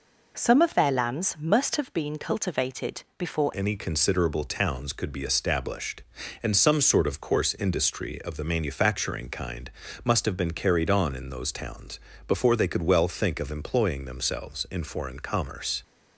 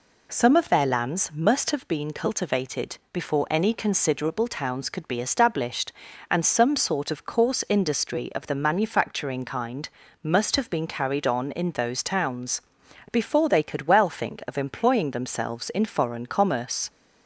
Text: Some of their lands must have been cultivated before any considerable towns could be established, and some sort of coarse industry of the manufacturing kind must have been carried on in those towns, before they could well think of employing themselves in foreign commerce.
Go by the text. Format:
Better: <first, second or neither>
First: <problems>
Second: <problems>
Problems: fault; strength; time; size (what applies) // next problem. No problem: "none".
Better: second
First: changes voice at "any"; from 3.5 s on; 12.3 s long // pauses between "kind" and "must"; slight; at 9.7 s; 0.34 s long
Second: pauses between "kind" and "must"; slight; at 9.8 s; 0.34 s long